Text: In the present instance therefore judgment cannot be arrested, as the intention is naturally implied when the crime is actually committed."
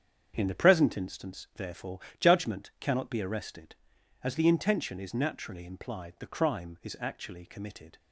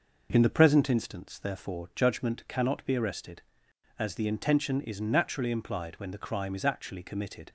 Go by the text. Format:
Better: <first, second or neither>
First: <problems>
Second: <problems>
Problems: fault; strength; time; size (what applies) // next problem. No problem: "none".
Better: second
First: starts louder than the rest; strong; until 1.3 s; 7.5 dB // pauses between "therefore" and "judgment"; slight; at 2.0 s; 0.18 s long // skips "when"; at 6.1 s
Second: none